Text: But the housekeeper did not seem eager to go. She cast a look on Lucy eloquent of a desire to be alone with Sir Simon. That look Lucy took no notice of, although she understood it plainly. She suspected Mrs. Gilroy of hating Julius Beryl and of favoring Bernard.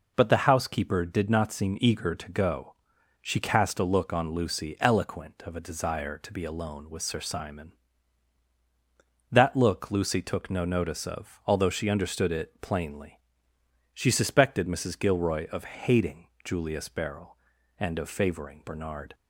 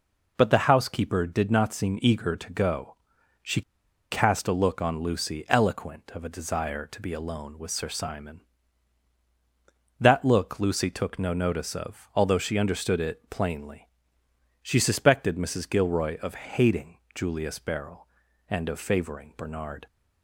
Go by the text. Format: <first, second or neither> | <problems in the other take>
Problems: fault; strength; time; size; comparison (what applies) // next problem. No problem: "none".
first | pauses between "She" and "cast"; noticeable; at 3.6 s; 0.50 s long // pauses between "hating" and "Julius"; slight; at 16.9 s; 0.16 s long; slight in the first